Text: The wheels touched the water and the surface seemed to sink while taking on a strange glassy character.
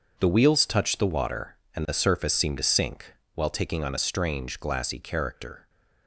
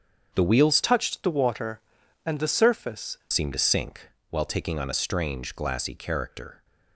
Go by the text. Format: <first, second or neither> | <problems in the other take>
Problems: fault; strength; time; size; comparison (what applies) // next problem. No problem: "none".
first | starts louder than the rest; strong; until 1.3 s; 7.5 dB; also in the first // changes voice from "touched" to "surface"; from 0.8 to 3.1 s; 2.3 s long // pauses between "sink" and "while"; slight; at 4.0 s; 0.22 s long; slight in the first